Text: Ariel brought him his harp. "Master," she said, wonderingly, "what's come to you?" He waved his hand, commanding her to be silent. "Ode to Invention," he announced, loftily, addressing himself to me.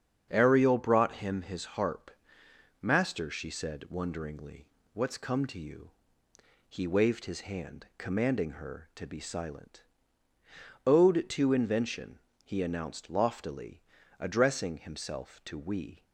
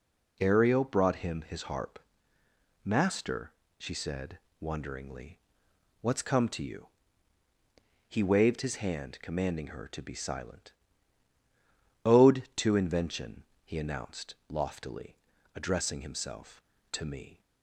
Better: second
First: starts louder than the rest; strong; until 1.3 s; 7.5 dB // says "we" for "me"; at 15.5 s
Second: none

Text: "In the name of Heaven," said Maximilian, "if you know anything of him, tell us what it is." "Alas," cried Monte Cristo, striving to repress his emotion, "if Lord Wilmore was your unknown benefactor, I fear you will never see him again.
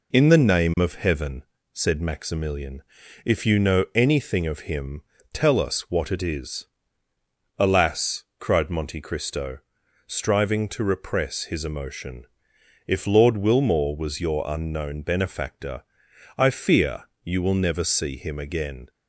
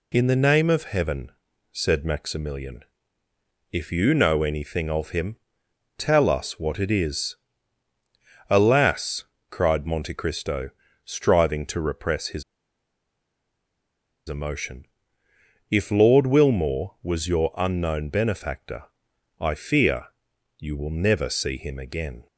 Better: first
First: pauses between "fear" and "you"; slight; at 17.0 s; 0.18 s long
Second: pauses between "his" and "emotion"; strong; at 12.4 s; 1.8 s long // pauses between "fear" and "you"; noticeable; at 20.0 s; 0.50 s long

